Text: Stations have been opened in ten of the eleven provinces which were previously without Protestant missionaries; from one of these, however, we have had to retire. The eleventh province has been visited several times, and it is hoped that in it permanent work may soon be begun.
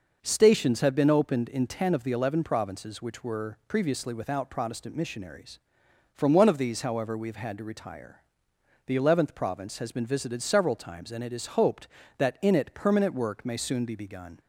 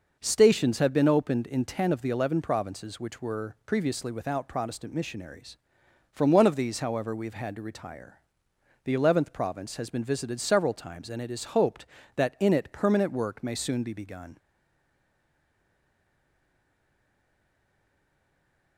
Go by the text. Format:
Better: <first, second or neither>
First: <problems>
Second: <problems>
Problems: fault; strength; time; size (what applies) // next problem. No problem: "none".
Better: first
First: none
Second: stays silent after the last word; strong; from 14.3 s on; 4.4 s long